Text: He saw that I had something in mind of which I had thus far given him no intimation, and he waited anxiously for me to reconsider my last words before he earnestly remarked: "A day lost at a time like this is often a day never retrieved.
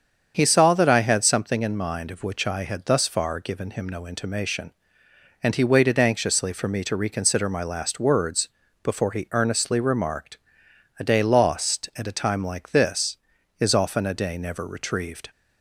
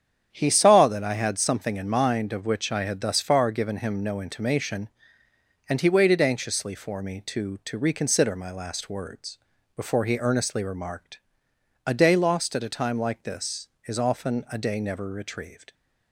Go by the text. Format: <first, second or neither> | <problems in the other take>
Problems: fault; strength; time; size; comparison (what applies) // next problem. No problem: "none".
first | starts louder than the rest; strong; until 1.3 s; 8.5 dB; strong in the first // says "to" twice; at 7.6 s // pauses between "words" and "before"; at 9.3 s; 0.38 s long; slight in the first